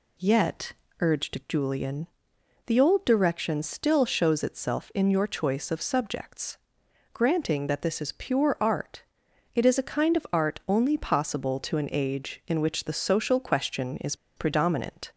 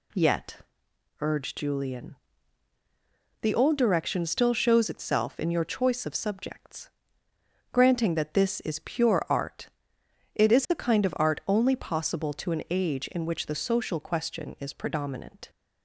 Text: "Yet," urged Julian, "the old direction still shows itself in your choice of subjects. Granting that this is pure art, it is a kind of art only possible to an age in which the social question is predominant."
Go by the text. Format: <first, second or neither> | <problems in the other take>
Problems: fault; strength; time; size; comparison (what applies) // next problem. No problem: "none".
second | pauses between "is" and "predominant"; slight; at 14.1 s; 0.21 s long